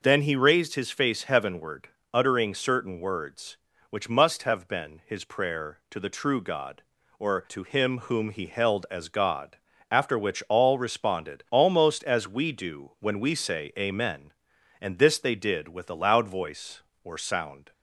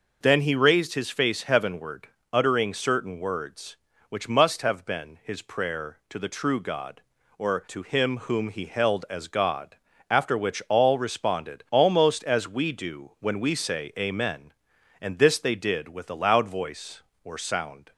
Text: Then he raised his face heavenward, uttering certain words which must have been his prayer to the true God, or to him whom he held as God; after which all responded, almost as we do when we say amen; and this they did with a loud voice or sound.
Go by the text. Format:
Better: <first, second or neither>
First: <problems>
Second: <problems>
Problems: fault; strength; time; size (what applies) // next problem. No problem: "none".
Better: neither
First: none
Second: none